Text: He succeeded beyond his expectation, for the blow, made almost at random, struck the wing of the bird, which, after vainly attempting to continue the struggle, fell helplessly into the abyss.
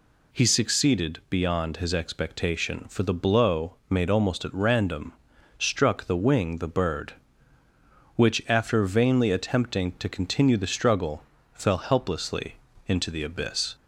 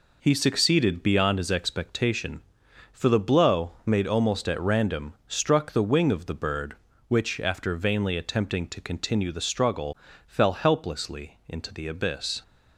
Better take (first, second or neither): second